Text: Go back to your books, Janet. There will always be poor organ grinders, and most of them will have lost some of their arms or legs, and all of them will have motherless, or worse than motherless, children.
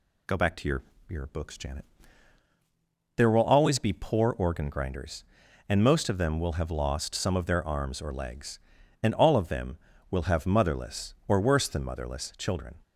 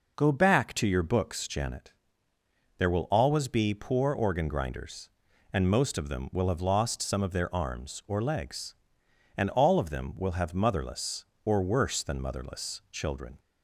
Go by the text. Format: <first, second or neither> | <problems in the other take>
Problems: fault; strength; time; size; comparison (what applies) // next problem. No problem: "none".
second | says "your" twice; at 1.0 s